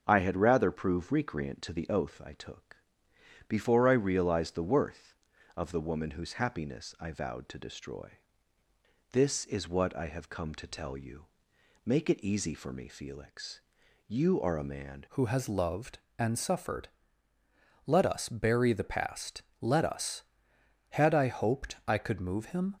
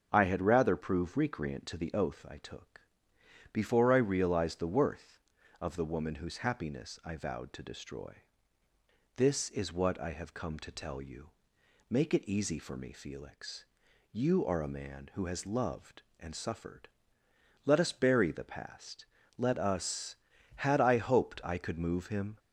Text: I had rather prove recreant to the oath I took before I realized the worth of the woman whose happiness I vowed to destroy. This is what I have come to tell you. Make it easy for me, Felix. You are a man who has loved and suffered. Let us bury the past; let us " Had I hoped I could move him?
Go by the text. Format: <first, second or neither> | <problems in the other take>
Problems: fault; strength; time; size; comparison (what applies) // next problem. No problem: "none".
second | starts louder than the rest; until 1.0 s; 6.5 dB; also in the second // pauses between "took" and "before"; noticeable; at 2.7 s; 0.72 s long; noticeable in the second // changes voice at "who"; from 15.0 s on; 7.7 s long